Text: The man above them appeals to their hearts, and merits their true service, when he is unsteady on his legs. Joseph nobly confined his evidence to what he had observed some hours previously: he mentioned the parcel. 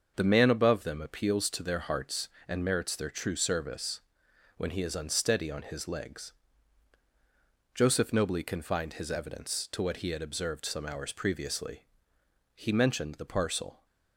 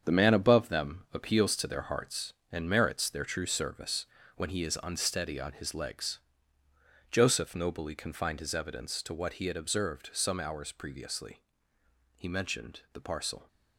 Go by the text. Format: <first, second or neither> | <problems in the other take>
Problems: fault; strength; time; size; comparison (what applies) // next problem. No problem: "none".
first | gets quieter; strong; throughout; 8.5 dB // starts louder than the rest; strong; until 1.0 s; 7.5 dB; also in the first